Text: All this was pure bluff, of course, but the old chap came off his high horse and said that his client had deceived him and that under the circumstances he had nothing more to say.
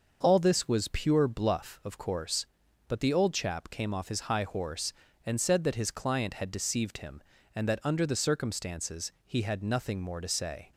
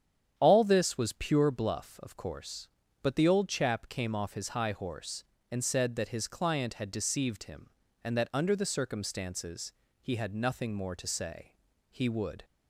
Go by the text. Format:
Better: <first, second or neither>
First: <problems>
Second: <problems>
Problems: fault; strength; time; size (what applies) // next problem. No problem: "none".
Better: first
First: starts louder than the rest; noticeable; until 1.2 s; 6 dB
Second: starts louder than the rest; strong; until 1.3 s; 9 dB // pauses between "circumstances" and "he"; slight; at 9.7 s; 0.30 s long // goes on to say "He would"; from 11.9 s on; 0.54 s long